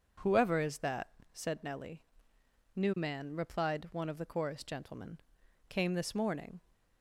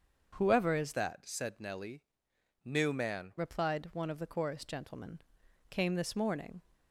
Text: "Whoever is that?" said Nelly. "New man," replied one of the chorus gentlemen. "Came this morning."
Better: first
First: none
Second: starts louder than the rest; until 1.3 s; 6.5 dB // changes voice from "that" to "man"; from 0.9 to 3.3 s; 2.4 s long

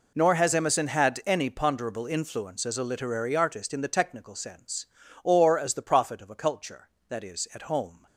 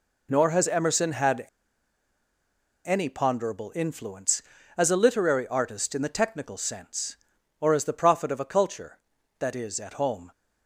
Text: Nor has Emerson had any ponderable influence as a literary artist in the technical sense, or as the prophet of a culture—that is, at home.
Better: first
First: none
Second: pauses between "had" and "any"; strong; at 1.4 s; 1.4 s long

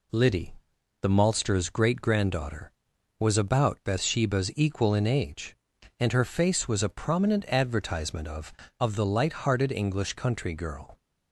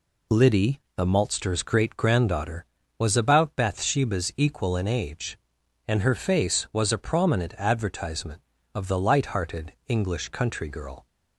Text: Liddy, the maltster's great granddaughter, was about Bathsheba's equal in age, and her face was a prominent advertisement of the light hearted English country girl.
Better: second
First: says "of" twice; at 8.7 s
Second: none

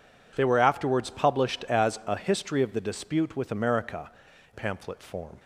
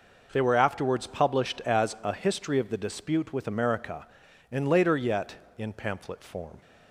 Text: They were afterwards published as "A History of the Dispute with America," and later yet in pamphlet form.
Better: second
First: skips "and later yet in"; at 4.3 s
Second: none

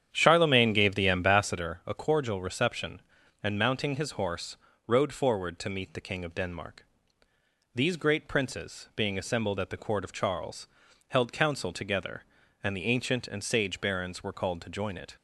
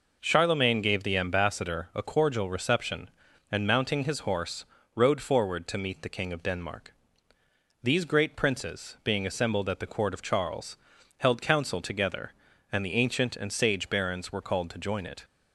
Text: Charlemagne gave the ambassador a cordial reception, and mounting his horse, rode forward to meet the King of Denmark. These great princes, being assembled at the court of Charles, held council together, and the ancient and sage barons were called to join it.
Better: second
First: starts louder than the rest; strong; until 1.6 s; 9 dB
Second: none

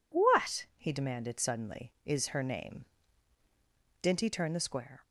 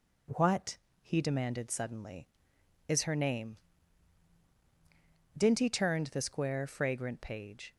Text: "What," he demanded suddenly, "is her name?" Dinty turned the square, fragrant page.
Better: second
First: stops before "fragrant page"; at 5.0 s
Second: none

